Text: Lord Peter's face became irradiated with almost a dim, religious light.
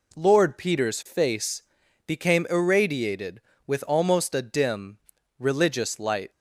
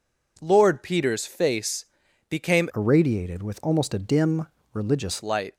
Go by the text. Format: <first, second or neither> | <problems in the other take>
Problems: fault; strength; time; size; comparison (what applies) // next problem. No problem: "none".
first | pauses between "face" and "became"; at 1.8 s; 0.44 s long; also in the first // changes voice from "irradiated" to "religious"; from 2.7 to 5.2 s; 2.5 s long